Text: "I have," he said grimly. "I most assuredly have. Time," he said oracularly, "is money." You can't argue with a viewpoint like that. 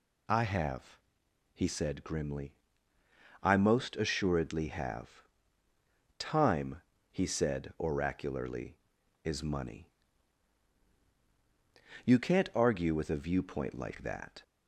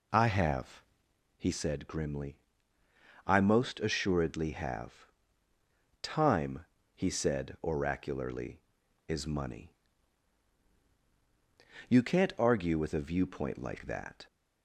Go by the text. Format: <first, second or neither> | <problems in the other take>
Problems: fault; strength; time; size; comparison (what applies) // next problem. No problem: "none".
first | starts louder than the rest; slight; until 1.3 s; 3 dB